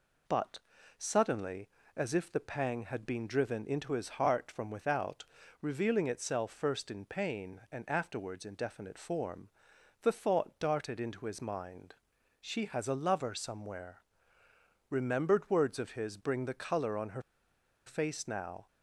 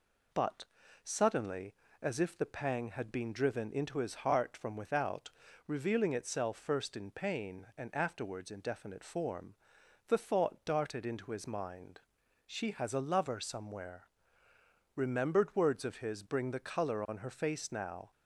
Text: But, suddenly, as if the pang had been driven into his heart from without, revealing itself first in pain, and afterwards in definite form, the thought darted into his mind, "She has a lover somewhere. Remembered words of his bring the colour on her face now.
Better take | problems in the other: second | pauses between "her" and "face"; noticeable; at 17.2 s; 0.64 s long

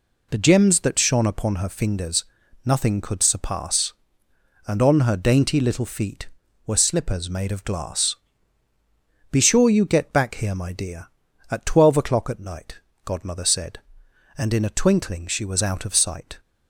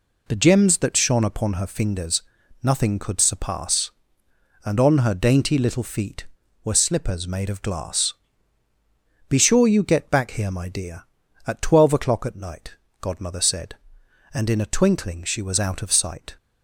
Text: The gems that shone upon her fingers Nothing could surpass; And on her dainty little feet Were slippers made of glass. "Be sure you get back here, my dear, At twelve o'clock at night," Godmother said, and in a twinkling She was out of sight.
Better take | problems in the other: neither | pauses between "fingers" and "Nothing"; the same in both

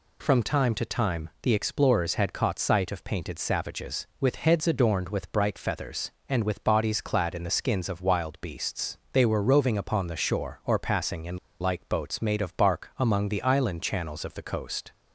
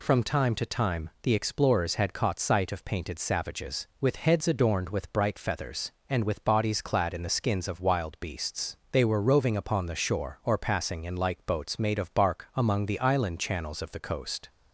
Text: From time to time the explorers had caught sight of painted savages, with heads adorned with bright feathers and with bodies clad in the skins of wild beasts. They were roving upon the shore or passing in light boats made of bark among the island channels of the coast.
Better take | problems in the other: second | pauses between "in" and "light"; slight; at 11.3 s; 0.23 s long

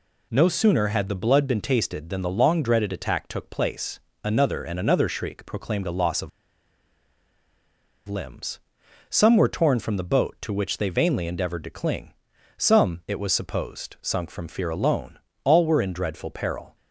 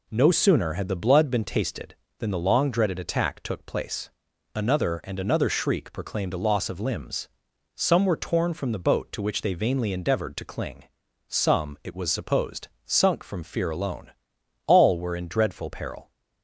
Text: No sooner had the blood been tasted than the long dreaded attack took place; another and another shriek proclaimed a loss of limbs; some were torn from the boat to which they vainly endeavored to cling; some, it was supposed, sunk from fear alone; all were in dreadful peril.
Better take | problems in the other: second | pauses between "of" and "limbs"; strong; at 6.2 s; 1.7 s long

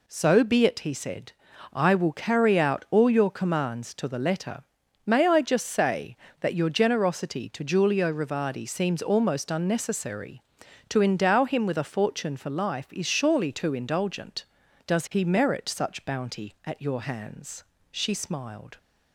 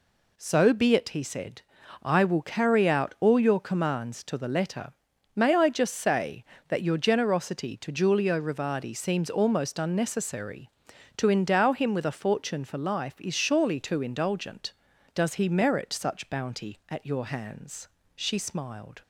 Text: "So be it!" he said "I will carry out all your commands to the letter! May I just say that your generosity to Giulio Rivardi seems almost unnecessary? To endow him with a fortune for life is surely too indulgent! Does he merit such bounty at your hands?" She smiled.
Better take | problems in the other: neither | pauses between "said" and "I"; the same in both

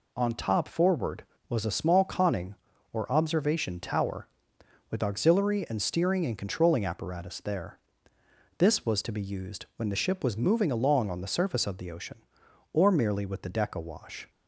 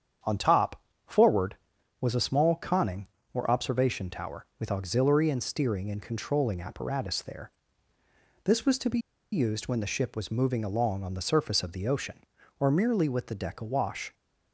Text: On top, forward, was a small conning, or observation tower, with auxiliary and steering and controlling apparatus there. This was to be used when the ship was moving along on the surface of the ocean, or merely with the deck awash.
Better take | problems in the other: first | starts louder than the rest; strong; until 1.5 s; 8 dB // pauses between "be" and "used"; slight; at 8.9 s; 0.34 s long

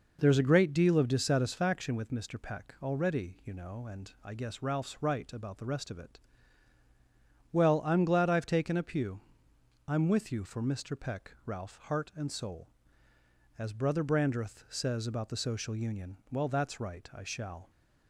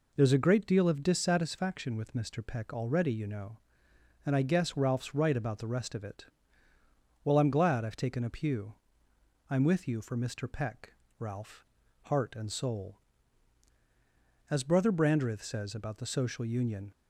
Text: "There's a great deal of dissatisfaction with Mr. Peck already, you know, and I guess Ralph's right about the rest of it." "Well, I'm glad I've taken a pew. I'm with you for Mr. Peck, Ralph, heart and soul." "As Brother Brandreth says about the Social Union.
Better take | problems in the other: second | goes on to say "Well that's right I shall"; from 16.2 s on; 1.4 s long

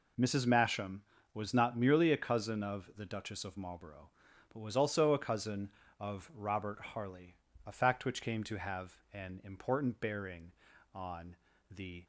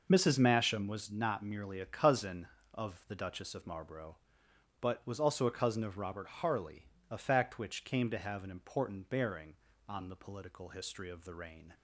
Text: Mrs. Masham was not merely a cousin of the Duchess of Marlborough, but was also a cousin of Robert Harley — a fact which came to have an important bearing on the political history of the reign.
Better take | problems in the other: second | pauses between "have" and "an"; slight; at 8.9 s; 0.16 s long // pauses between "on" and "the"; slight; at 11.3 s; 0.34 s long // stops before "political history of the reign"; at 12.0 s

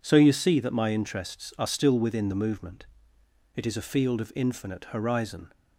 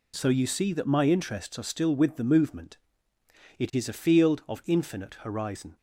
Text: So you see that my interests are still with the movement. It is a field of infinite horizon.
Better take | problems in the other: second | says "within" for "with"; at 1.9 s

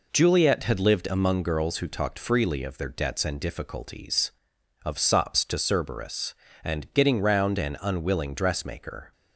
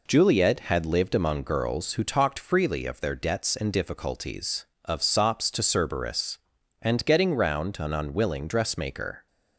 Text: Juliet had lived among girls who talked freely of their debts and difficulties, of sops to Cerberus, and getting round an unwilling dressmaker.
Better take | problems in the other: neither | none

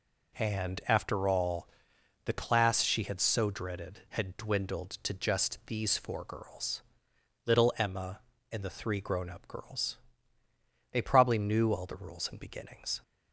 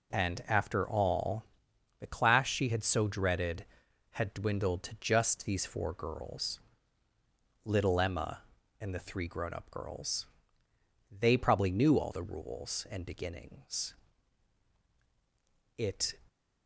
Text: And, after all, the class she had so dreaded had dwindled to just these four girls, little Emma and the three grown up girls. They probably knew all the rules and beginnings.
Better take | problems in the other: first | goes on to say "It"; slight; from 15.7 s on; 0.38 s long

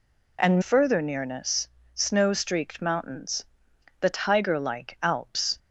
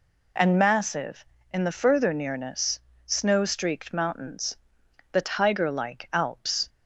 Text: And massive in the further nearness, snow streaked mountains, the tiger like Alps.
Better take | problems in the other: second | skips "massive in the"; at 0.6 s

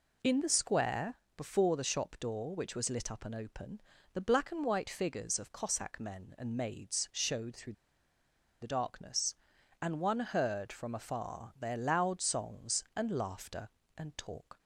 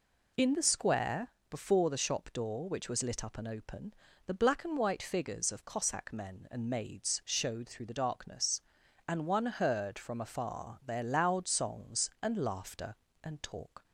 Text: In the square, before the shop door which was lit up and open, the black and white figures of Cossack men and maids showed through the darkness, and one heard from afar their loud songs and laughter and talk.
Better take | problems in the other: second | pauses between "through" and "the"; noticeable; at 7.7 s; 0.89 s long

